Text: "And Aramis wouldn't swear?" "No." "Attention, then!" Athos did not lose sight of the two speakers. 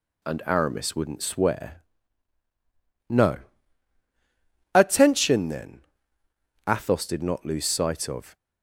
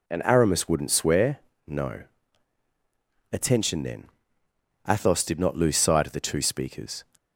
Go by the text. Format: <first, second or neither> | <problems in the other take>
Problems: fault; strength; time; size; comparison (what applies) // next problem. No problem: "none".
second | stops before "the two speakers"; at 8.3 s